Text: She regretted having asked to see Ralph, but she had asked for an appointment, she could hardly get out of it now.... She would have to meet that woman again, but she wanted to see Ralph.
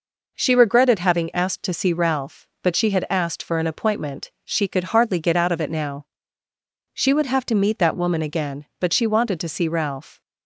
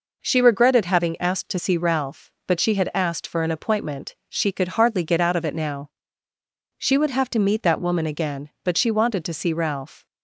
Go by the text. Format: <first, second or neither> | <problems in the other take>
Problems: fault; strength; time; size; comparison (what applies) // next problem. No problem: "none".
neither | none